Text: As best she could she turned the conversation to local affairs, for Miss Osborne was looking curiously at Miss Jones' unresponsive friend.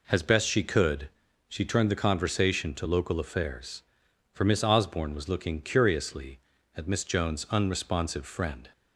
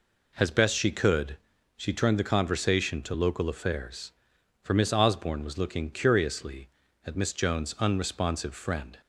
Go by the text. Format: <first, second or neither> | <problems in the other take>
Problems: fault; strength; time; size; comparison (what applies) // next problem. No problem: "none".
neither | pauses between "could" and "she"; the same in both